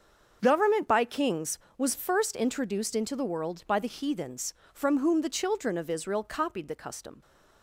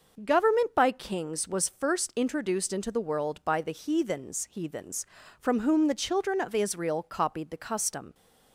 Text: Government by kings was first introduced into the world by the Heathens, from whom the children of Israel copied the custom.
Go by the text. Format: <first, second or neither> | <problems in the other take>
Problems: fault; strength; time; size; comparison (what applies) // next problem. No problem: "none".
first | starts louder than the rest; noticeable; until 1.2 s; 6 dB; also in the first // says "Heathens" twice; at 4.4 s